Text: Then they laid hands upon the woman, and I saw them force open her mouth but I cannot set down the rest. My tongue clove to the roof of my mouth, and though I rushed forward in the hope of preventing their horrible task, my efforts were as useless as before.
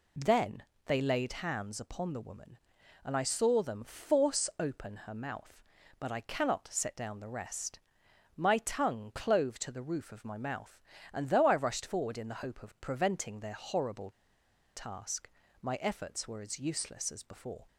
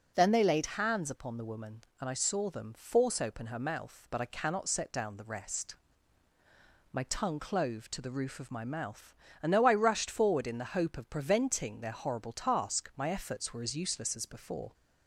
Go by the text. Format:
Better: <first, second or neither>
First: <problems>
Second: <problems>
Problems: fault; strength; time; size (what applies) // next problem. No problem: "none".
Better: second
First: pauses between "Then" and "they"; slight; at 0.6 s; 0.24 s long // pauses between "horrible" and "task"; noticeable; at 14.1 s; 0.63 s long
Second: none